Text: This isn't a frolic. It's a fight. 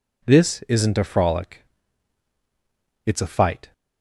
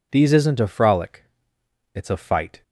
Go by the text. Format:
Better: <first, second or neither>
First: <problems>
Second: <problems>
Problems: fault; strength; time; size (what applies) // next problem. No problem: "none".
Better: first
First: none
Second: says "These" for "This"; at 0.1 s